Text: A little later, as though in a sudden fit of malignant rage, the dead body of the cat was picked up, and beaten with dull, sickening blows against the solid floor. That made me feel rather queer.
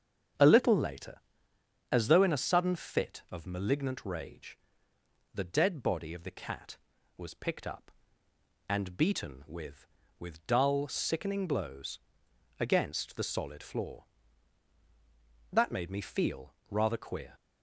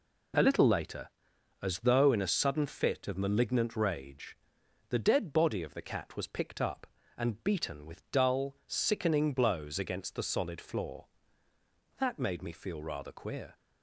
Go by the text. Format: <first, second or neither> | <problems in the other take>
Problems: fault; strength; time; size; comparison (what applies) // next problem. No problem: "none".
second | starts louder than the rest; until 2.0 s; 7 dB // says "with" twice; at 10.1 s // pauses between "blows" and "against"; noticeable; at 11.9 s; 0.60 s long // pauses between "feel" and "rather"; slight; at 16.5 s; 0.16 s long